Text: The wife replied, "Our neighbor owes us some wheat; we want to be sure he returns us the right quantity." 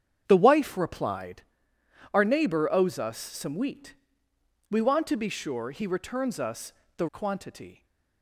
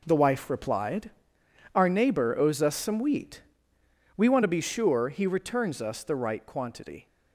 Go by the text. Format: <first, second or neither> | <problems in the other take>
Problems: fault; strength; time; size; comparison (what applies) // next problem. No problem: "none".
second | starts louder than the rest; strong; until 1.2 s; 8 dB // pauses between "us" and "the"; slight; at 6.7 s; 0.24 s long // skips "right"; at 7.0 s